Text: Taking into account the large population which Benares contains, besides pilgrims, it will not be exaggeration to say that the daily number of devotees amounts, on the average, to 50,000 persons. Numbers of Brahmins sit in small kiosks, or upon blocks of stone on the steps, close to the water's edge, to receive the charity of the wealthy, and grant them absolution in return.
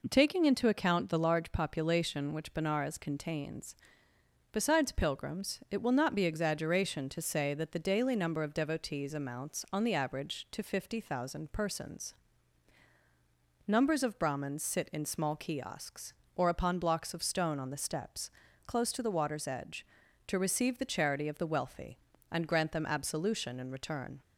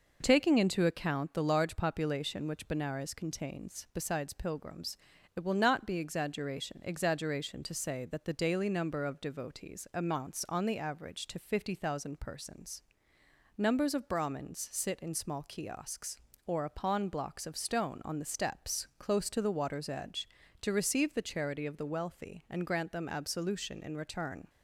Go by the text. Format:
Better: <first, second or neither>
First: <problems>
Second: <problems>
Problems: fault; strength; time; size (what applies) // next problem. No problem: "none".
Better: first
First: none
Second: says "exaggeration" twice; at 6.8 s